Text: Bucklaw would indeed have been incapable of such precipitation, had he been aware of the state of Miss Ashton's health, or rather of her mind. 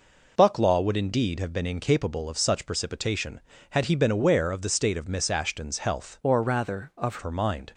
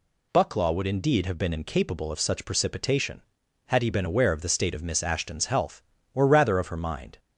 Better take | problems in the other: second | changes voice from "or" to "of"; from 6.2 to 7.1 s; 0.9 s long

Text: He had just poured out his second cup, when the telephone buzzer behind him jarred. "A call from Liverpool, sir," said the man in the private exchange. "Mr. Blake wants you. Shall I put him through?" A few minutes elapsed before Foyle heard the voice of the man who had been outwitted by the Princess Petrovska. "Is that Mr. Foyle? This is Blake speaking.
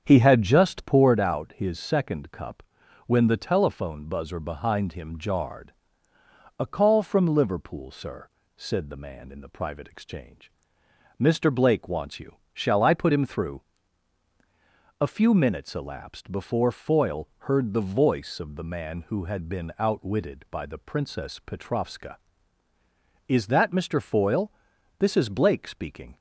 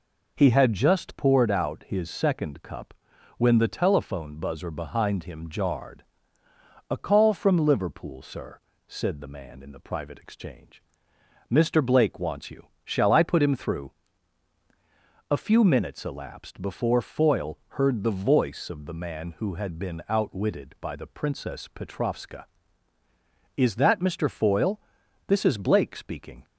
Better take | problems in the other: second | starts louder than the rest; strong; until 1.3 s; 7.5 dB

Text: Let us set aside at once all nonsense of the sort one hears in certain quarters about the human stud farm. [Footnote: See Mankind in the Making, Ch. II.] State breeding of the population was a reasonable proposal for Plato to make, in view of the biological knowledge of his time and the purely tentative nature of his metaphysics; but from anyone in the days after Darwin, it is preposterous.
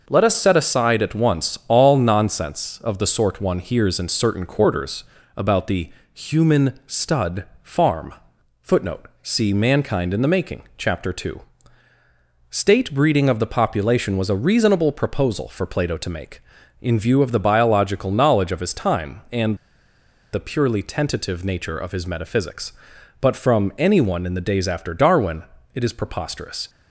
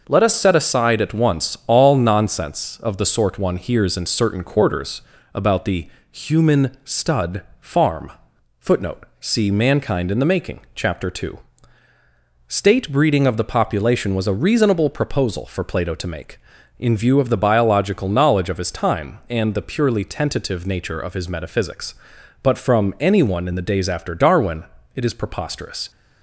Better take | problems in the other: second | pauses between "quarters" and "about"; slight; at 5.0 s; 0.34 s long; slight in the second // pauses between "the" and "human"; slight; at 5.8 s; 0.24 s long; slight in the second // pauses between "stud" and "farm"; slight; at 7.4 s; 0.20 s long; slight in the second // pauses between "and" and "the"; noticeable; at 19.5 s; 0.77 s long

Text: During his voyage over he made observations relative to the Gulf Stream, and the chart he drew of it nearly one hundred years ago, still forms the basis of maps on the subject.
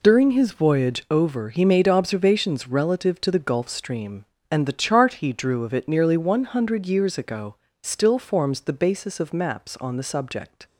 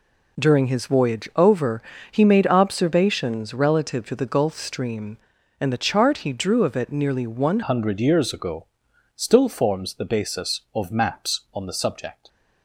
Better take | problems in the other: first | pauses between "over" and "he"; slight; at 1.8 s; 0.30 s long // changes voice at "hundred"; from 7.6 s on; 4.6 s long

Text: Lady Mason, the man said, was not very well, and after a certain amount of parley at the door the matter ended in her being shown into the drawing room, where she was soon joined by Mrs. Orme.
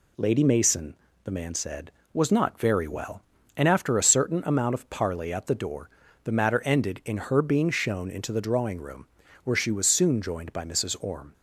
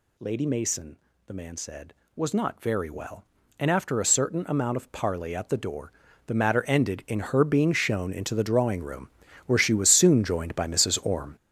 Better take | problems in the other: first | gets louder; strong; throughout; 9.5 dB // pauses between "door" and "the"; slight; at 5.9 s; 0.36 s long; slight in the first

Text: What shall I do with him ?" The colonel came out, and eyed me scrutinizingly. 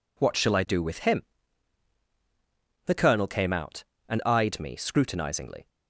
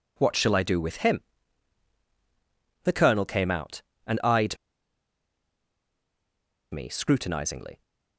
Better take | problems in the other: first | pauses between "eyed" and "me"; strong; at 4.5 s; 2.1 s long

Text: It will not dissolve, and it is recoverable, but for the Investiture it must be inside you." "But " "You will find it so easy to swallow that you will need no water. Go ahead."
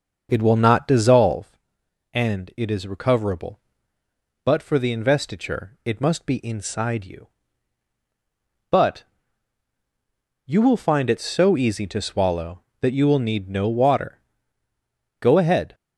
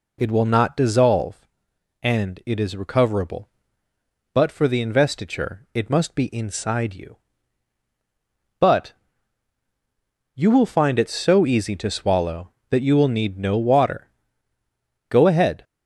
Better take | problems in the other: second | starts louder than the rest; until 1.5 s; 7 dB

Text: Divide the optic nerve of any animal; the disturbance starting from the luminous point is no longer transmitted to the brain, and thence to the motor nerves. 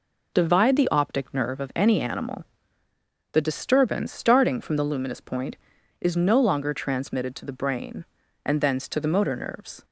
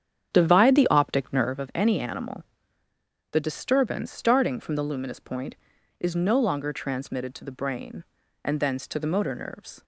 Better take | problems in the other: first | starts louder than the rest; strong; until 1.7 s; 9 dB

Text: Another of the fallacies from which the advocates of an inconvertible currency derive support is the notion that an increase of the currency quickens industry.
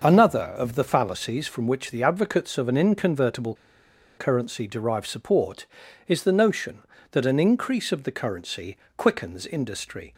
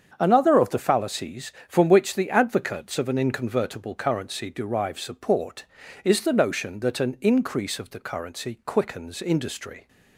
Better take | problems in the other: second | starts louder than the rest; noticeable; until 1.1 s; 6 dB; strong in the second // pauses between "inconvertible" and "currency"; noticeable; at 3.5 s; 0.62 s long // pauses between "currency" and "quickens"; slight; at 8.7 s; 0.18 s long

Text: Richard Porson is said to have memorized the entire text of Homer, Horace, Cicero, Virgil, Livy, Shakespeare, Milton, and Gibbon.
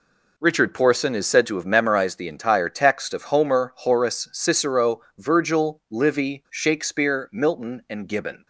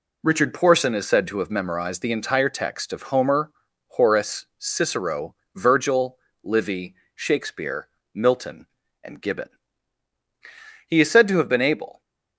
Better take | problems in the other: first | goes on to say "He is said to have been able"; noticeable; from 10.8 s on; 1.1 s long

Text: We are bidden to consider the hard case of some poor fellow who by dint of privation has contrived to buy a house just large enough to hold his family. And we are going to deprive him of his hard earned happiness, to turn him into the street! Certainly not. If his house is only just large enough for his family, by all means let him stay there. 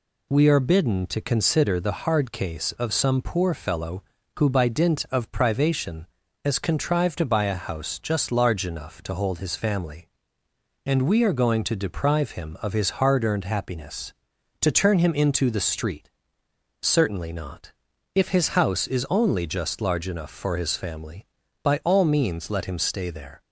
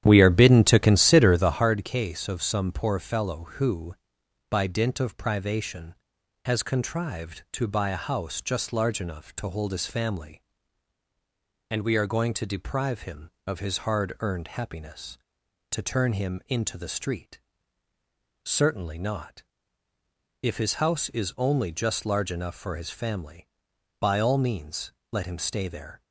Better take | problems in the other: first | starts louder than the rest; strong; until 1.7 s; 10.5 dB // pauses between "means" and "let"; slight; at 24.9 s; 0.20 s long

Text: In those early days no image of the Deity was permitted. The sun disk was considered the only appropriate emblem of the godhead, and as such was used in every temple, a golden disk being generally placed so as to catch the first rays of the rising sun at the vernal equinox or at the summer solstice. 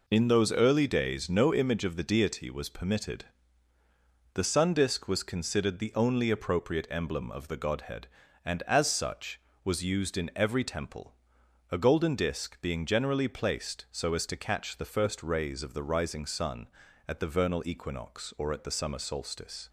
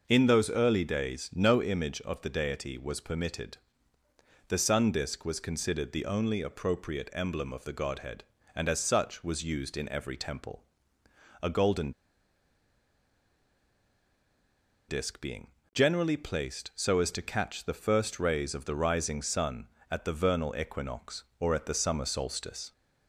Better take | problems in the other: first | pauses between "golden" and "disk"; strong; at 11.9 s; 2.9 s long // pauses between "being" and "generally"; slight; at 15.4 s; 0.24 s long

